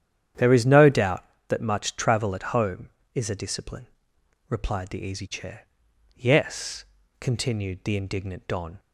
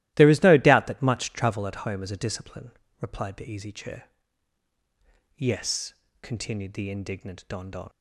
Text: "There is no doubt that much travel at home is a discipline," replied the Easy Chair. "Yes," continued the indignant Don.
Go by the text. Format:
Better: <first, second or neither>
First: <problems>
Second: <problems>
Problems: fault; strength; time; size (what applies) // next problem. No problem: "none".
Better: first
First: starts louder than the rest; strong; until 1.6 s; 9.5 dB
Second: starts louder than the rest; strong; until 1.1 s; 16 dB // says "Don" twice; at 7.6 s